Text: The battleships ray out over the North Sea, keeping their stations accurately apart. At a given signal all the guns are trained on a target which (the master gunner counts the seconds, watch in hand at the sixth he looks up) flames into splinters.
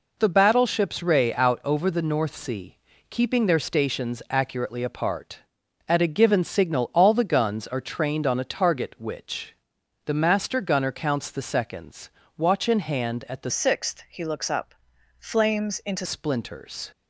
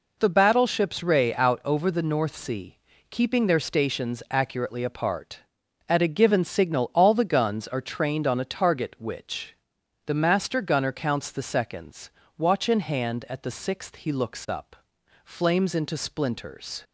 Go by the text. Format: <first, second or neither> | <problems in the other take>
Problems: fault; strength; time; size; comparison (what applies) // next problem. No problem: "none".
second | changes voice from "sixth" to "into"; from 13.5 to 16.0 s; 2.5 s long